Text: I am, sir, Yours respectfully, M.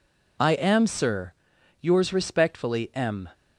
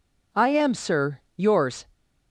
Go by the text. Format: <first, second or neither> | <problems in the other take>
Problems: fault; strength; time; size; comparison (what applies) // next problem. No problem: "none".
first | stops before "respectfully M"; at 1.9 s